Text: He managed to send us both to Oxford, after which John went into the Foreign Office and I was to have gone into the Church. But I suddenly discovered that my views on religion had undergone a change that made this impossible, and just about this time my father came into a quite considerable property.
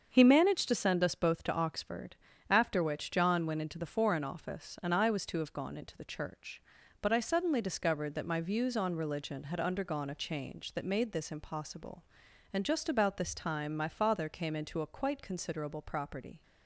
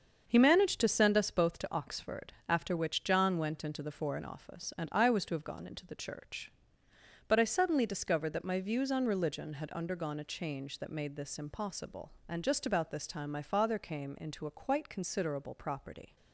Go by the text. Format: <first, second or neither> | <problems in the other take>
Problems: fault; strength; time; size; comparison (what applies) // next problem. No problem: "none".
neither | starts louder than the rest; the same in both